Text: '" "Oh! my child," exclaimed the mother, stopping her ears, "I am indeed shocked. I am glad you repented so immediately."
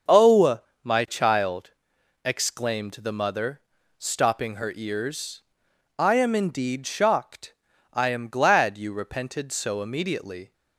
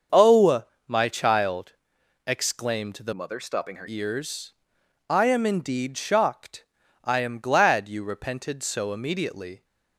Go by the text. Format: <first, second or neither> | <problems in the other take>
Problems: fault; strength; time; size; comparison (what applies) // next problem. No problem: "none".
first | starts louder than the rest; until 1.3 s; 6.5 dB; also in the first // changes voice from "mother" to "her"; from 3.1 to 3.8 s; 0.7 s long